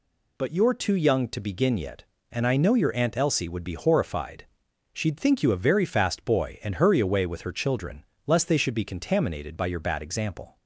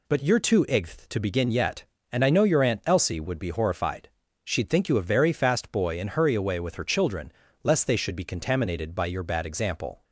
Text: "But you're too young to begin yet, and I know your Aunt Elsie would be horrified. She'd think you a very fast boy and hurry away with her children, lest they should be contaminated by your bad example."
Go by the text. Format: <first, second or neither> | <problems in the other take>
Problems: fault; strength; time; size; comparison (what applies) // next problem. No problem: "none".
first | says "igth" for "young"; at 0.6 s